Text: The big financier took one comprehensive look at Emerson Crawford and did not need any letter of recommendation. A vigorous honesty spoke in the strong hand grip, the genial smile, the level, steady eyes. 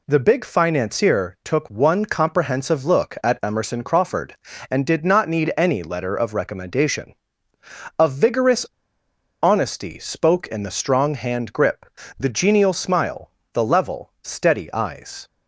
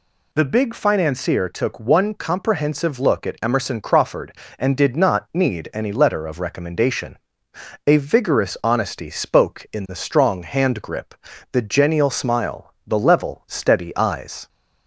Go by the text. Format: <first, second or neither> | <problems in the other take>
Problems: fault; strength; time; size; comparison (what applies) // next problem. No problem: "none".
second | pauses between "vigorous" and "honesty"; noticeable; at 8.6 s; 0.77 s long